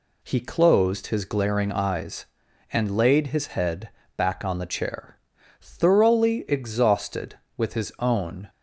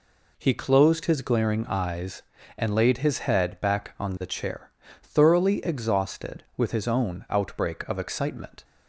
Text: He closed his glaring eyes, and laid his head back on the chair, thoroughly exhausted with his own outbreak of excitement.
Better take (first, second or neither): second